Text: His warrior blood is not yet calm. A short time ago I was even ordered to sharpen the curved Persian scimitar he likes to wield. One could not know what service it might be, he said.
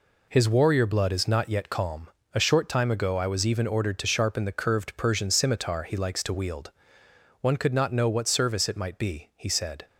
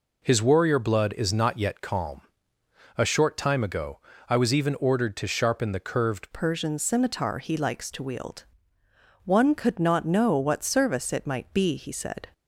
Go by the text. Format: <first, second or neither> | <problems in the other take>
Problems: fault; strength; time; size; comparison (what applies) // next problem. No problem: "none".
first | pauses between "ago" and "I"; slight; at 3.9 s; 0.30 s long // changes voice at "Persian"; from 6.3 s on; 5.9 s long